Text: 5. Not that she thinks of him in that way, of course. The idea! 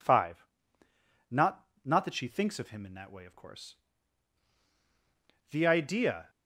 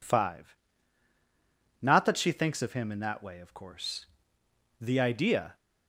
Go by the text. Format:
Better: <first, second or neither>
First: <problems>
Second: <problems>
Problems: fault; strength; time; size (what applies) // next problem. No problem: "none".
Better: second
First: says "Not" twice; at 1.8 s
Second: none